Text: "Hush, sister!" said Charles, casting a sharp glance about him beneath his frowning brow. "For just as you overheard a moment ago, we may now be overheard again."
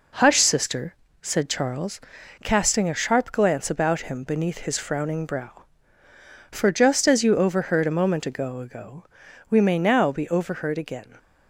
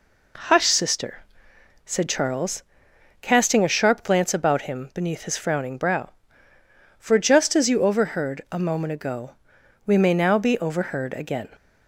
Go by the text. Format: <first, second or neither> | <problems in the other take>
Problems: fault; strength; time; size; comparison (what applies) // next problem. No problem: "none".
second | says "ago" twice; at 8.5 s